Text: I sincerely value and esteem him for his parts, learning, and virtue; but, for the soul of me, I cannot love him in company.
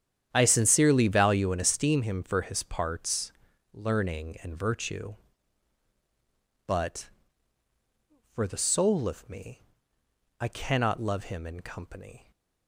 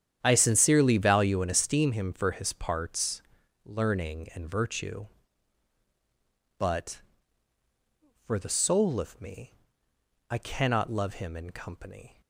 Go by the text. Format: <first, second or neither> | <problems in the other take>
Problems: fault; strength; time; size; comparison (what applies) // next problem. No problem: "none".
neither | starts louder than the rest; strong; the same in both